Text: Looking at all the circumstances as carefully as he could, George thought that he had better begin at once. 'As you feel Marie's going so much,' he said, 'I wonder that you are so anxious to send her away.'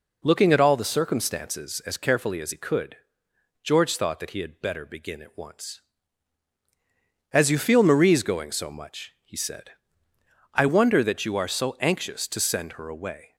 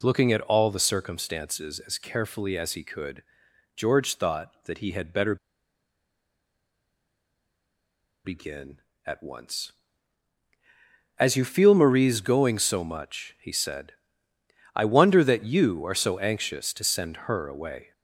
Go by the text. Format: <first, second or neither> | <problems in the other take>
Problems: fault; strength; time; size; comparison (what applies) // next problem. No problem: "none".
first | pauses between "better" and "begin"; strong; at 5.3 s; 2.8 s long